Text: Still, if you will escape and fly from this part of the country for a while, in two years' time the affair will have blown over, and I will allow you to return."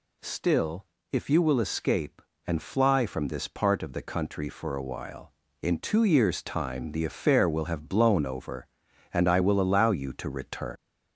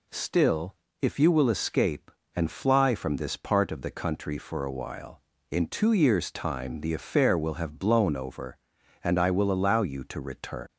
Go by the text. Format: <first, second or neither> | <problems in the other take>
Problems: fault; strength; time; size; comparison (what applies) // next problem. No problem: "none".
second | gets louder; slight; throughout; 3 dB